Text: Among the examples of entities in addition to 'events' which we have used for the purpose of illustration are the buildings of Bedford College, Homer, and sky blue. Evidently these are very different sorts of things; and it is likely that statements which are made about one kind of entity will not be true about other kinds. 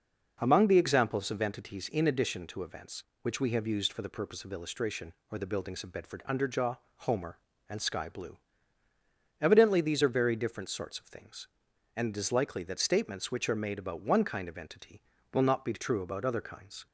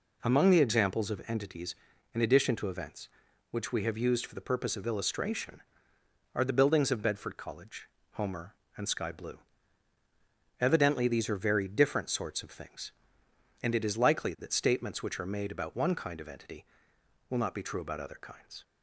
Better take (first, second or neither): second